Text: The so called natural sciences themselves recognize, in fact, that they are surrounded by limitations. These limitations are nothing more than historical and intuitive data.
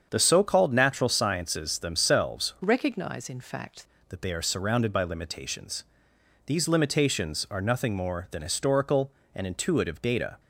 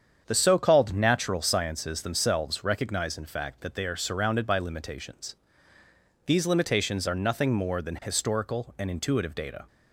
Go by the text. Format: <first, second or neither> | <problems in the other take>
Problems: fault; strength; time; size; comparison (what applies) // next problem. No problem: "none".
second | starts louder than the rest; strong; until 1.1 s; 7.5 dB; strong in the second // changes voice from "recognize" to "fact"; from 2.6 to 3.8 s; 1.2 s long